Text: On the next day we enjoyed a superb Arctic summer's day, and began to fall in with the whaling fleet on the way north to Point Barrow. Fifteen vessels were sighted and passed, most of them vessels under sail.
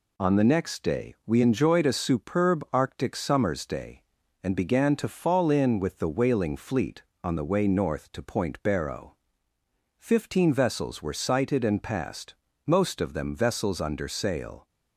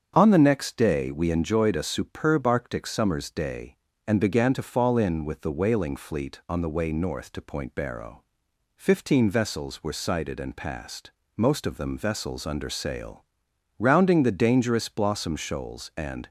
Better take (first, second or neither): first